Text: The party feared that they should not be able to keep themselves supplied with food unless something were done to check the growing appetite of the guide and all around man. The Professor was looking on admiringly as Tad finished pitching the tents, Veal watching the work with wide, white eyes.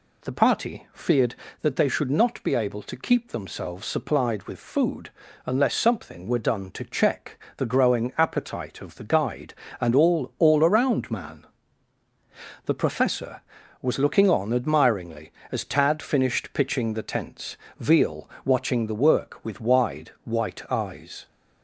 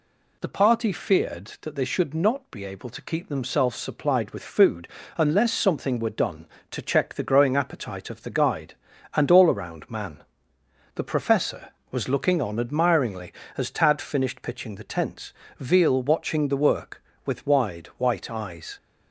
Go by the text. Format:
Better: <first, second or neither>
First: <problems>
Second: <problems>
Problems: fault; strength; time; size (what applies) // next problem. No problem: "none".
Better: second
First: pauses between "food" and "unless"; slight; at 5.1 s; 0.34 s long // says "all" twice; at 10.3 s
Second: pauses between "food" and "unless"; slight; at 4.8 s; 0.30 s long